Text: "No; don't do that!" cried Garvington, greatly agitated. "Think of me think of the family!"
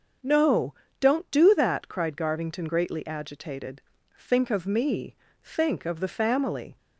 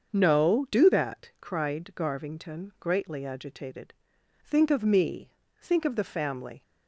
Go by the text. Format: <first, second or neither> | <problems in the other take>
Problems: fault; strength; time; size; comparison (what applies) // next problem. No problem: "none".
first | starts louder than the rest; until 1.1 s; 6.5 dB; also in the first // skips "don't"; at 0.6 s // pauses between "me" and "think"; slight; at 5.3 s; 0.30 s long; slight in the first